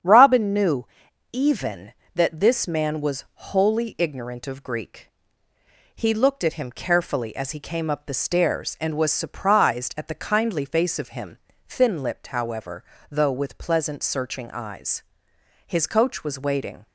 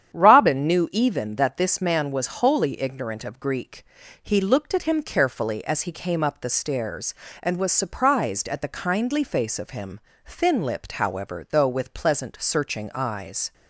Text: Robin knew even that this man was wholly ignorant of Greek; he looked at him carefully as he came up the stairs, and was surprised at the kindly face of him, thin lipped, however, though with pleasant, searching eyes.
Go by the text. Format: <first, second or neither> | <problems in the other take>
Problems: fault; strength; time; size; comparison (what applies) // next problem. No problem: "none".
second | starts louder than the rest; strong; until 1.4 s; 8 dB; strong in the second // pauses between "knew" and "even"; noticeable; at 0.8 s; 0.46 s long // goes on to say "His coach was waiting"; noticeable; from 15.6 s on; 1.1 s long